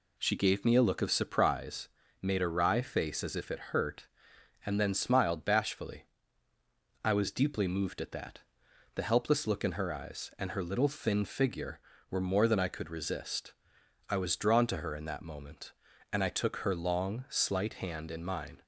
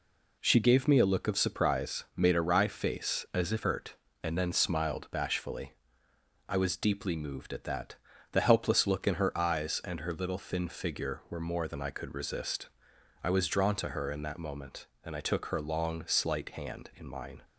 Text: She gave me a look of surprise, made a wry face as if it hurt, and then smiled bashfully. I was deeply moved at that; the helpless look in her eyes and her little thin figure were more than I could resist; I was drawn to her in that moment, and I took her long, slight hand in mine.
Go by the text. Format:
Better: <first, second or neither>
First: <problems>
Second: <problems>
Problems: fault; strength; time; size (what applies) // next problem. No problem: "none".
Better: first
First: none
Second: skips "it"; at 3.6 s